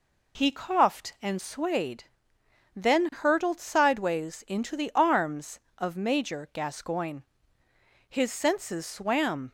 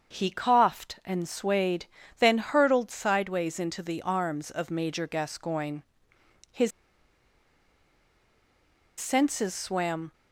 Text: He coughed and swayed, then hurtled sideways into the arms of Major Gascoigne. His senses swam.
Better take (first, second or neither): first